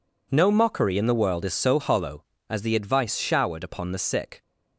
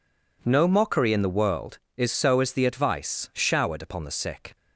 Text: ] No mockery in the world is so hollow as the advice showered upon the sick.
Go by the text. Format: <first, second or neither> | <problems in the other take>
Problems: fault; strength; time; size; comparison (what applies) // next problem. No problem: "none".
first | skips "hollow"; at 2.4 s